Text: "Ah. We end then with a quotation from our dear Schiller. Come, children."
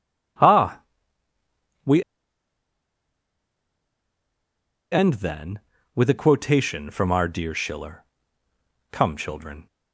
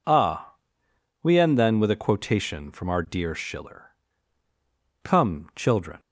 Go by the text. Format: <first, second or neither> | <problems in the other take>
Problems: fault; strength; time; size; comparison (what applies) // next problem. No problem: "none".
second | pauses between "We" and "end"; strong; at 2.0 s; 2.8 s long